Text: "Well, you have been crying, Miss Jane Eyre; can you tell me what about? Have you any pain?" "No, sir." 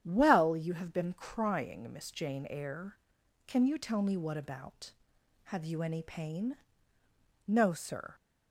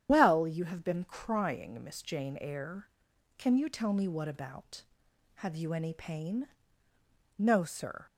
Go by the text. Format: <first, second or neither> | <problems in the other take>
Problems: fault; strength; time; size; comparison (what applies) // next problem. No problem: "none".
first | loses the start of "Well"; at 0.0 s; 140 ms // starts louder than the rest; strong; until 1.1 s; 9.5 dB; strong in the first